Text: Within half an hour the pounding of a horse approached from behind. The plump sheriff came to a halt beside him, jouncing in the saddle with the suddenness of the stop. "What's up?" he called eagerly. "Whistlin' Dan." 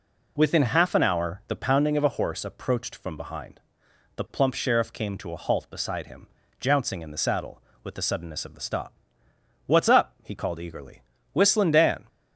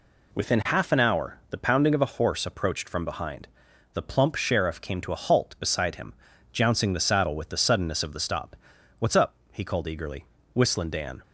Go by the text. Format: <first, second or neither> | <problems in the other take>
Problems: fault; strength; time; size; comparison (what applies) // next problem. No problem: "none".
first | skips "in"; at 6.9 s